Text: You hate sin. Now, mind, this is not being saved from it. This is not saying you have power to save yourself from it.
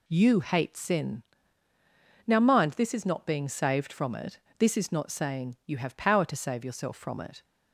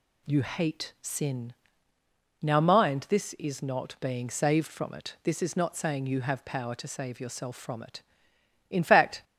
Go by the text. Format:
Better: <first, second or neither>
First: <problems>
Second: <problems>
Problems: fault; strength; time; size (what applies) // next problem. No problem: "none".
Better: first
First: none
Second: goes on to say "In fact"; from 8.6 s on; 0.54 s long